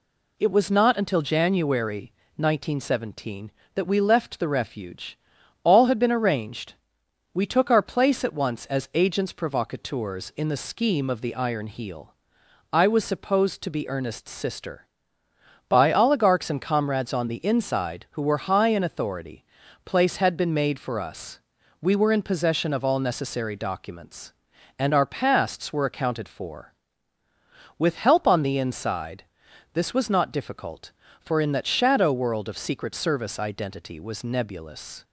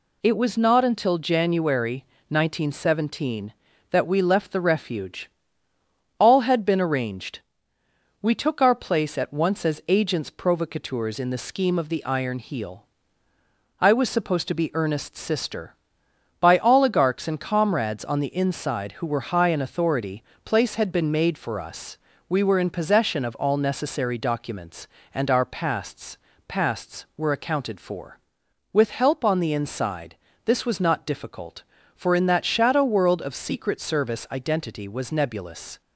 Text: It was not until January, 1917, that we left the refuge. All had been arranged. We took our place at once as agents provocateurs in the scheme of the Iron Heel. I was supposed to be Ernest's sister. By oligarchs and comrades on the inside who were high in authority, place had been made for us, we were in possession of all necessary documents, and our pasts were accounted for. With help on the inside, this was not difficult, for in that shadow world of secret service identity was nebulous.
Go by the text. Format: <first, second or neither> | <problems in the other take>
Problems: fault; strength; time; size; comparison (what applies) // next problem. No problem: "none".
first | says "pasts" twice; at 26.4 s